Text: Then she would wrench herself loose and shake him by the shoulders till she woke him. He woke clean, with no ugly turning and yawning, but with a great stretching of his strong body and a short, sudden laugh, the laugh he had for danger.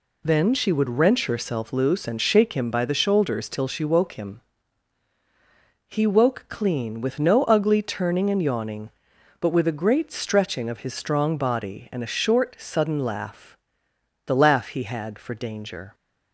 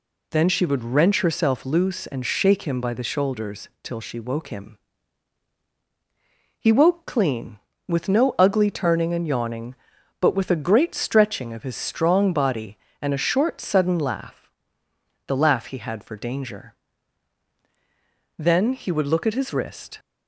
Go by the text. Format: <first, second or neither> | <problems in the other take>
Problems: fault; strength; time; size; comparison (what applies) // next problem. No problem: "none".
first | goes on to say "Then he would look at his wrist"; from 18.3 s on; 1.6 s long